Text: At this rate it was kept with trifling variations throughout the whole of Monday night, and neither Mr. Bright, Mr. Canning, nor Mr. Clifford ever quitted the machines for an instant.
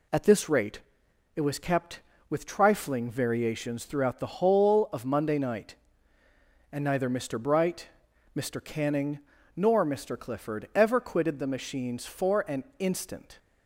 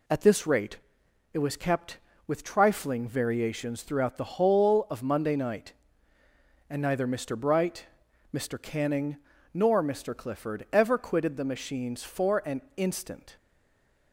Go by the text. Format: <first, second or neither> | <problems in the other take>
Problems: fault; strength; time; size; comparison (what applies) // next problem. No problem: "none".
first | pauses between "rate" and "it"; noticeable; at 0.7 s; 0.54 s long; noticeable in the first // stays silent after the last word; slight; from 13.3 s on; 0.8 s long